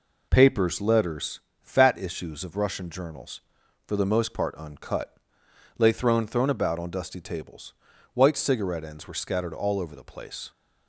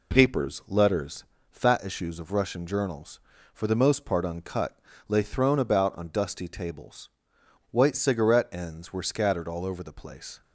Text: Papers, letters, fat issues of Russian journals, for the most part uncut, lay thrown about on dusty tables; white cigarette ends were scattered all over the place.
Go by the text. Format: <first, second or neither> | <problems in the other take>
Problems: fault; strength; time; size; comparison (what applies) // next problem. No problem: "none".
second | says "thrown" twice; at 6.2 s